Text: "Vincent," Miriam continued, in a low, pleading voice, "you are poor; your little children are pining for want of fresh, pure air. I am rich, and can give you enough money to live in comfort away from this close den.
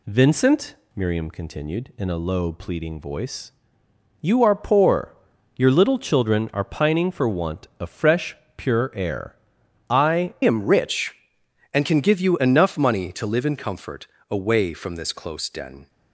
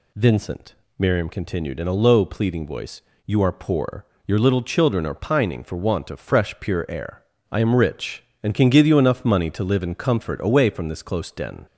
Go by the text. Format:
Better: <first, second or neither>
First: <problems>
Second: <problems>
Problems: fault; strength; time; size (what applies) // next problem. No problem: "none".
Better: second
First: changes voice at "am"; from 10.4 s on; 5.4 s long // pauses between "comfort" and "away"; slight; at 14.0 s; 0.22 s long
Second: none